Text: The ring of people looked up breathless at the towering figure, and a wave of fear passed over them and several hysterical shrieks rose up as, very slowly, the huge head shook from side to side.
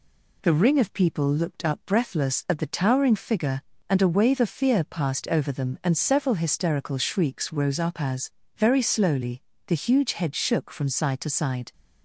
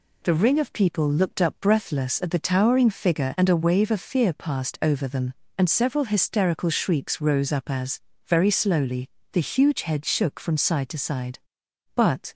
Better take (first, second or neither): first